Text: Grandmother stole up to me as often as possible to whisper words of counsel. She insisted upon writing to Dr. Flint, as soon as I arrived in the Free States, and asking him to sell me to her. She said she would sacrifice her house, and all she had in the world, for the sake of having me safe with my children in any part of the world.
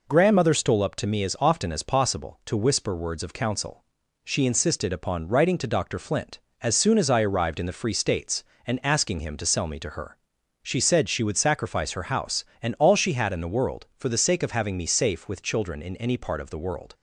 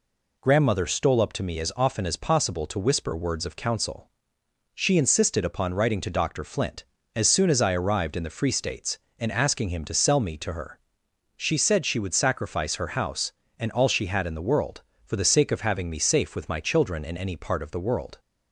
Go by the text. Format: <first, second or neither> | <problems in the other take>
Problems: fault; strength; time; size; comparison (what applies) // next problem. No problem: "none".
second | skips "my"; at 15.4 s